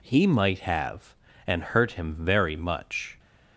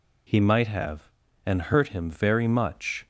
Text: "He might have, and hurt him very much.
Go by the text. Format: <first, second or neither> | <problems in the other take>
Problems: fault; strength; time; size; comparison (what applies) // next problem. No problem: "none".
neither | none